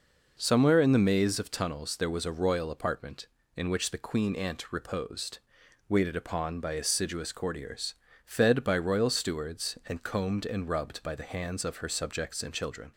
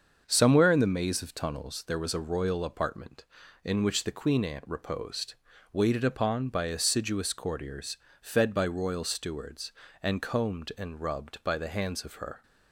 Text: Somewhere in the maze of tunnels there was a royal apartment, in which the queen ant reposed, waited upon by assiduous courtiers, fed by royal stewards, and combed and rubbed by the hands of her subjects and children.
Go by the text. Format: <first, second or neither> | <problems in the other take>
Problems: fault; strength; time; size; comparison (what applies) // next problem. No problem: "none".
first | starts louder than the rest; until 1.2 s; 6.5 dB // stops before "subjects and children"; at 12.4 s